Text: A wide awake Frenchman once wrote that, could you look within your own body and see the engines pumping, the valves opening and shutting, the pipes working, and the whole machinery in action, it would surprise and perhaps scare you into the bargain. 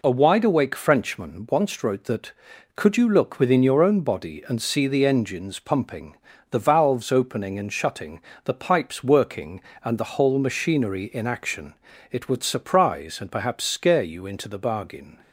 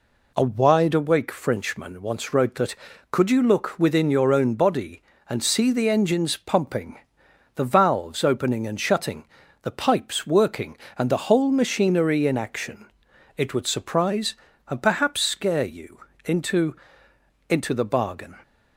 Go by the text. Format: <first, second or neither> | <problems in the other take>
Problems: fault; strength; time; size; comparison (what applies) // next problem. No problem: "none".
first | pauses between "you" and "into"; slight; at 15.9 s; 0.26 s long // says "into" twice; at 17.4 s